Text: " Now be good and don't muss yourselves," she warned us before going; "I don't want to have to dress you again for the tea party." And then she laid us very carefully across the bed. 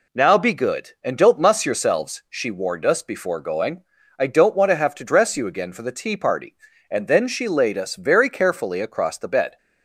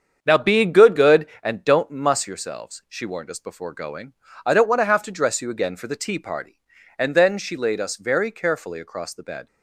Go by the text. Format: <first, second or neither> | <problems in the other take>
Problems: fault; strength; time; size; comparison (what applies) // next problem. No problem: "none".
first | starts louder than the rest; strong; until 1.2 s; 7.5 dB // says "good" twice; at 0.9 s